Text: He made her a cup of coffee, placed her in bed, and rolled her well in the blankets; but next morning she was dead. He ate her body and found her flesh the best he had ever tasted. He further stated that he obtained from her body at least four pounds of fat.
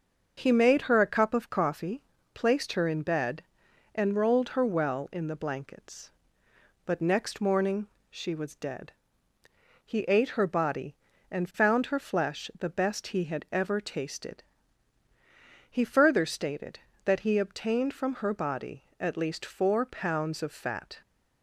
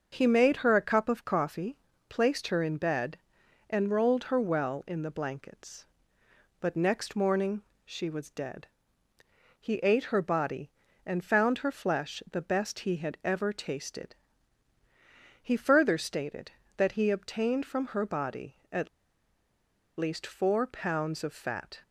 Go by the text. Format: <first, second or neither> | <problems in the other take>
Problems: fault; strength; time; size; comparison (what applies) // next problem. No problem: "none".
first | starts louder than the rest; until 1.1 s; 6.5 dB; also in the first // pauses between "morning" and "she"; slight; at 7.6 s; 0.20 s long; slight in the first // pauses between "at" and "least"; at 18.8 s; 1.1 s long